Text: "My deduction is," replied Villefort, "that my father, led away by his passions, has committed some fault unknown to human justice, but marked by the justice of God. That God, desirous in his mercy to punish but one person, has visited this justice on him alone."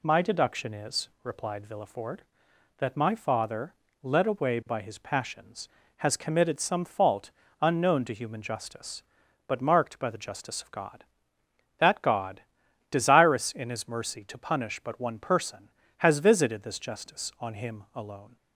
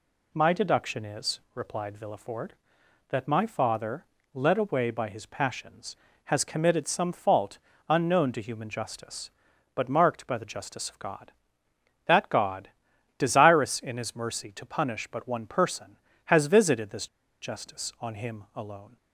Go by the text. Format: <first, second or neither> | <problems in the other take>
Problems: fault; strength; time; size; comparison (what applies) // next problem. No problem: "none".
first | pauses between "fault" and "unknown"; slight; at 7.5 s; 0.30 s long; slight in the first // pauses between "this" and "justice"; slight; at 17.0 s; 0.34 s long